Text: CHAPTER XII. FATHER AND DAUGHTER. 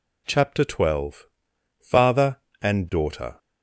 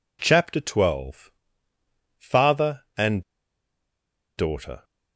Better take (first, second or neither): first